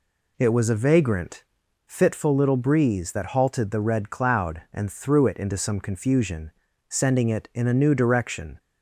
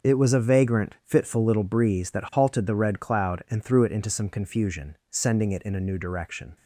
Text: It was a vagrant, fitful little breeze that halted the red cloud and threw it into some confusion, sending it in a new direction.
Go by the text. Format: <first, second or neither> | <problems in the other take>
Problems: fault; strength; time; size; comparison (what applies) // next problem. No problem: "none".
neither | none